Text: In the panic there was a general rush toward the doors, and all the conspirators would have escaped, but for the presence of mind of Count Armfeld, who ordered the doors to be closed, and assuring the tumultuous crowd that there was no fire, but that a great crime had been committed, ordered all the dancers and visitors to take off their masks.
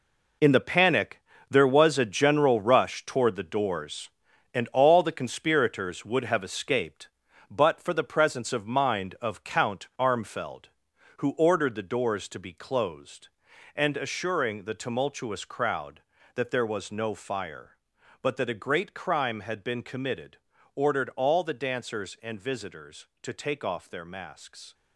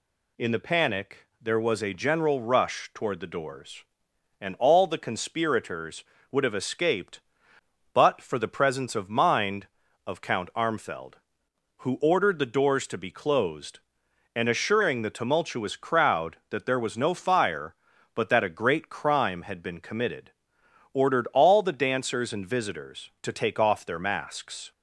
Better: second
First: gets quieter; strong; throughout; 10 dB // pauses between "panic" and "there"; slight; at 1.2 s; 0.28 s long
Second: none

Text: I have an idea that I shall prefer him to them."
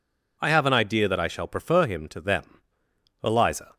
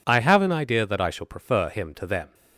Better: second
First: goes on to say "Eliza"; from 3.2 s on; 0.52 s long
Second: none

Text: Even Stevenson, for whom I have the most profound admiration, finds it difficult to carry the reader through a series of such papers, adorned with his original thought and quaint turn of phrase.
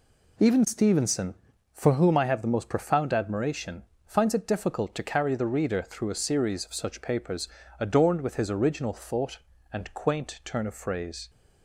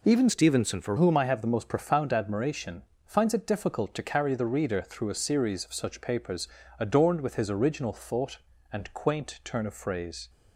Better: first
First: none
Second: changes voice from "Stevenson" to "for"; from 0.2 to 0.9 s; 0.7 s long

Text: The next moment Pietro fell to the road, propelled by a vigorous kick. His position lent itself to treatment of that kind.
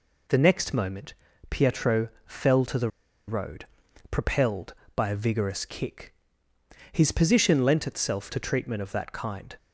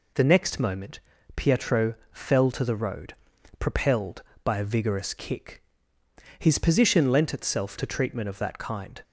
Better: second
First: pauses between "moment" and "Pietro"; slight; at 1.1 s; 0.36 s long // pauses between "Pietro" and "fell"; slight; at 2.0 s; 0.16 s long // pauses between "the" and "road"; at 2.8 s; 0.38 s long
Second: pauses between "moment" and "Pietro"; slight; at 0.9 s; 0.36 s long // pauses between "Pietro" and "fell"; slight; at 1.9 s; 0.16 s long

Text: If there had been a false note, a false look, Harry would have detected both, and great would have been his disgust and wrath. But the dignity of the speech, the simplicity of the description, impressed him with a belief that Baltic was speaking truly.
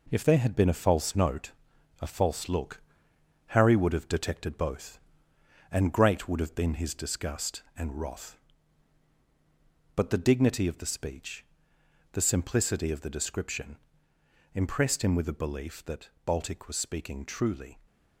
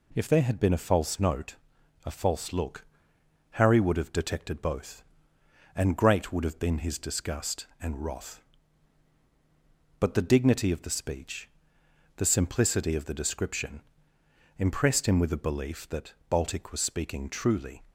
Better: second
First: gets quieter; noticeable; throughout; 5.5 dB // pauses between "that" and "Baltic"; slight; at 16.0 s; 0.16 s long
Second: pauses between "that" and "Baltic"; slight; at 16.1 s; 0.16 s long

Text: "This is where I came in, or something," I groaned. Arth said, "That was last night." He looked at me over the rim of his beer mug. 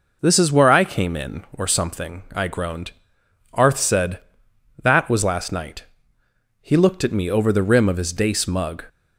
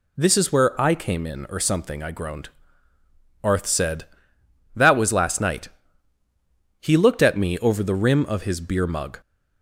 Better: second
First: says "dace" for "beer"; at 8.1 s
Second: none

